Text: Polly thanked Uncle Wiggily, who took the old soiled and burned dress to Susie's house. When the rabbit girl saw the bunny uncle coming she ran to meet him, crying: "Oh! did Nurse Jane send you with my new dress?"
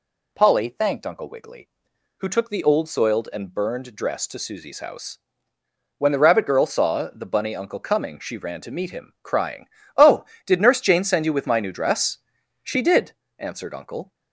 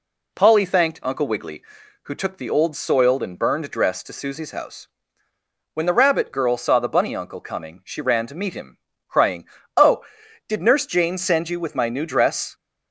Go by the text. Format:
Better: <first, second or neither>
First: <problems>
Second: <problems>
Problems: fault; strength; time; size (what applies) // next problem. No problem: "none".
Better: second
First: goes on to say "She did answered Uncle"; from 12.6 s on; 1.5 s long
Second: none